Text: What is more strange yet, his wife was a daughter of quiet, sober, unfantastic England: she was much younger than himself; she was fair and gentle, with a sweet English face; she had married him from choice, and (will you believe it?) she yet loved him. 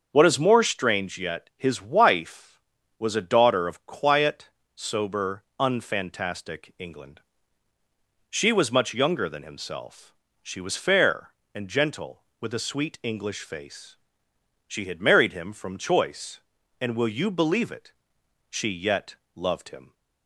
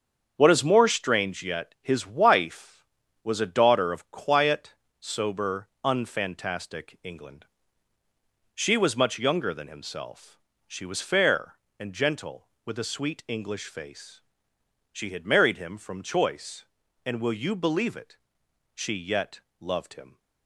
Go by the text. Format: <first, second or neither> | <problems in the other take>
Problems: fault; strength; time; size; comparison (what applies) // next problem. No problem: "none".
first | gets quieter; throughout; 6.5 dB // starts louder than the rest; strong; until 1.3 s; 7 dB; also in the first // pauses between "yet" and "loved"; slight; at 19.3 s; 0.22 s long; slight in the first